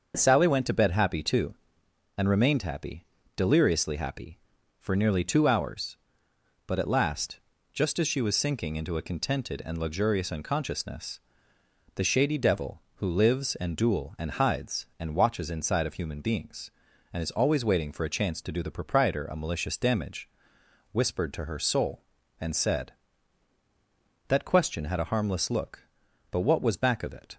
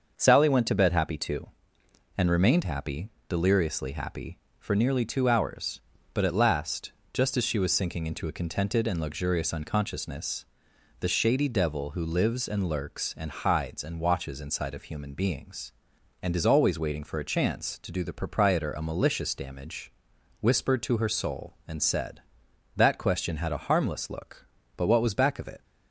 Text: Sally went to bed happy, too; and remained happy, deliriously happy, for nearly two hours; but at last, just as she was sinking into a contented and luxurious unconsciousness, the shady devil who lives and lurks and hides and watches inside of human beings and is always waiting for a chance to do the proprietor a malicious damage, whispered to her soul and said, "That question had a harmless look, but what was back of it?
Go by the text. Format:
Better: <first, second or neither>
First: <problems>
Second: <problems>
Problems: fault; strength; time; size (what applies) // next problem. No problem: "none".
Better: second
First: starts louder than the rest; until 1.2 s; 6.5 dB // says "duel" for "lurks"; at 13.7 s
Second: starts louder than the rest; until 1.1 s; 6.5 dB